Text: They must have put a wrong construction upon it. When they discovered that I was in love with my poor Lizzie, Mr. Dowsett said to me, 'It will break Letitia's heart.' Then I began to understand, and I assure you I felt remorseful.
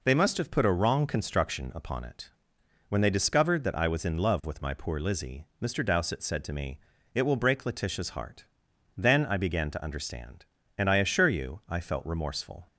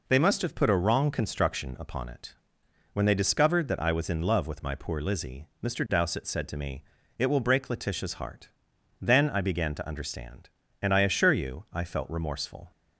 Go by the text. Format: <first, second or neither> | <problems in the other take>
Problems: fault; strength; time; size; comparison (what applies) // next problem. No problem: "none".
neither | none